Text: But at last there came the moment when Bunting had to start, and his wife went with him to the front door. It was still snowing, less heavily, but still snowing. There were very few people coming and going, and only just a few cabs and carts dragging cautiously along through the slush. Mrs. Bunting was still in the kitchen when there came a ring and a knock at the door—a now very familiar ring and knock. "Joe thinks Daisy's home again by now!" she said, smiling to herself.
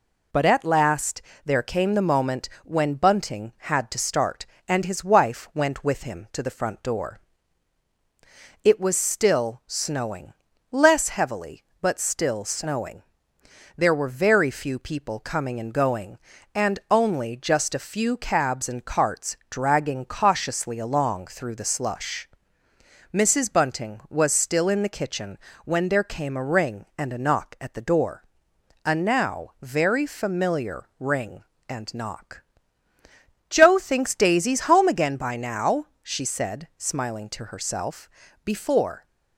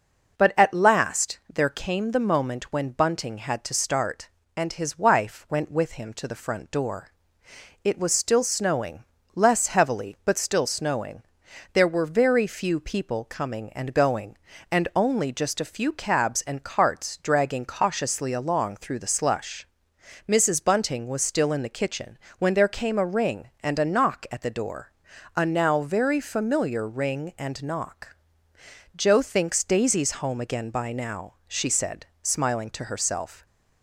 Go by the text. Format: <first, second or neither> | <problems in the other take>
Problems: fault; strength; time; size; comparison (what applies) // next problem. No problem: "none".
second | pauses between "last" and "there"; slight; at 1.2 s; 0.24 s long // pauses between "moment" and "when"; slight; at 2.4 s; 0.16 s long // pauses between "kitchen" and "when"; slight; at 25.3 s; 0.28 s long; slight in the second // goes on to say "Before"; noticeable; from 38.4 s on; 0.62 s long